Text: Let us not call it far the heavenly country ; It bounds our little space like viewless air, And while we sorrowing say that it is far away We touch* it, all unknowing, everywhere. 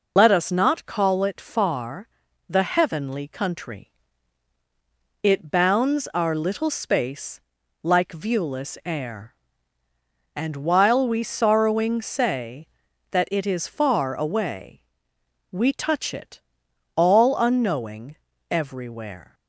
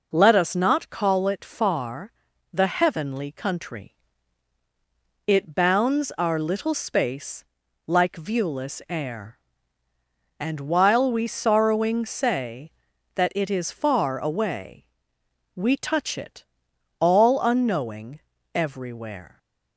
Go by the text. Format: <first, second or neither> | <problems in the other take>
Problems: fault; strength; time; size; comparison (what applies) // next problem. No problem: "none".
second | loses the start of "Let"; at 0.1 s; 70 ms // pauses between "far" and "the"; at 2.0 s; 0.40 s long; also in the second // pauses between "space" and "like"; at 7.4 s; 0.40 s long; also in the second // pauses between "away" and "We"; noticeable; at 14.7 s; 0.72 s long; noticeable in the second